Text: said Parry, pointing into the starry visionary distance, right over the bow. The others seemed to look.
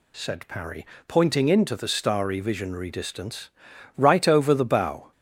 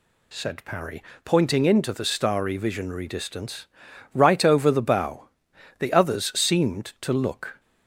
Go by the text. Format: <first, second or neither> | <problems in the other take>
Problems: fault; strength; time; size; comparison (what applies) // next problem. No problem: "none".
second | stops before "The others seemed to look"; at 5.1 s